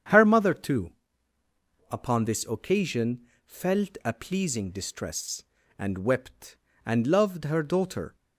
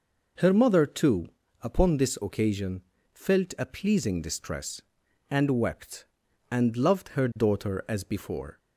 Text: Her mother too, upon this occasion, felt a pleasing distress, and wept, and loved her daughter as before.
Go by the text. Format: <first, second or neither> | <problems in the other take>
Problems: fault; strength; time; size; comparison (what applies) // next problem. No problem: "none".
second | starts louder than the rest; strong; until 2.0 s; 8 dB // stops before "as before"; at 8.1 s